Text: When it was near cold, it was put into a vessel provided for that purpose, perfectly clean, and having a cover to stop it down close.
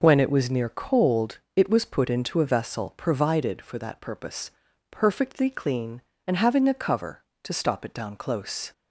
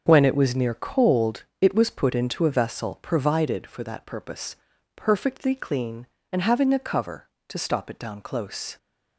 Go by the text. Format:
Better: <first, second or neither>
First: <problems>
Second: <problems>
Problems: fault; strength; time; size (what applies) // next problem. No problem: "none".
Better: first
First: none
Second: gets quieter; strong; throughout; 9.5 dB